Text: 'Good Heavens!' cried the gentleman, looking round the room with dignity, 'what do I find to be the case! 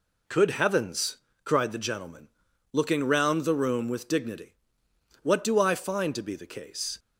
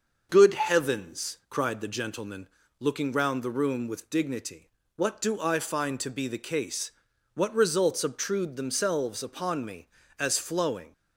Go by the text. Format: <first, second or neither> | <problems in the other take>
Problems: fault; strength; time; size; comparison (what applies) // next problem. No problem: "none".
first | starts louder than the rest; until 1.3 s; 6.5 dB // goes on to say "what results obtrude themselves upon me as flowing"; strong; from 7.3 s on; 3.5 s long